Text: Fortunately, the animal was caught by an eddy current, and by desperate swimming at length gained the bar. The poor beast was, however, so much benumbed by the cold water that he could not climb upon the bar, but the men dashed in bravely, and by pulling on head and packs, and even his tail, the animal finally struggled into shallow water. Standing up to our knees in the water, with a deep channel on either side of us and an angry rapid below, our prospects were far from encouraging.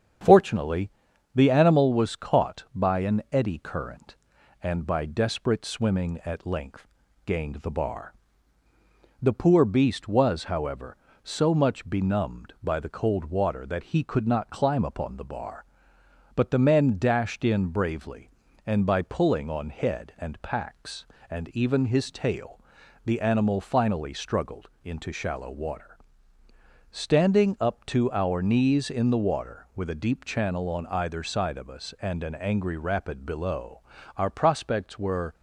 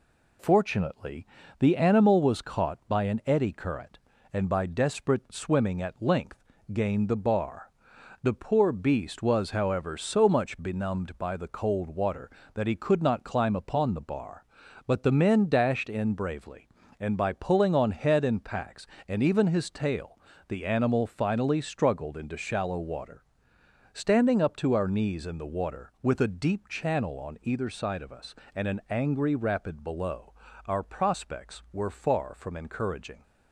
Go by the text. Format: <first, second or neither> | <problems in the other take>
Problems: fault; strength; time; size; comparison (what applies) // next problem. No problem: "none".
second | starts louder than the rest; strong; until 1.6 s; 8 dB // pauses between "length" and "gained"; at 6.8 s; 0.40 s long; slight in the second // pauses between "struggled" and "into"; slight; at 24.6 s; 0.16 s long // stops before "far from encouraging"; at 35.3 s